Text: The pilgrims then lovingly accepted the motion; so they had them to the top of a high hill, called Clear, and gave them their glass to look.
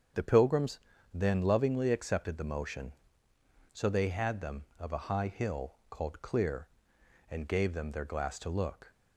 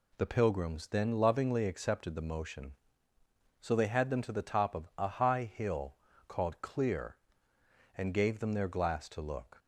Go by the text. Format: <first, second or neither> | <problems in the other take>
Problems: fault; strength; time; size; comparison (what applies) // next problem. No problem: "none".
second | starts louder than the rest; strong; until 1.5 s; 7.5 dB // pauses between "pilgrims" and "then"; slight; at 0.7 s; 0.34 s long // skips "to the top"; at 4.7 s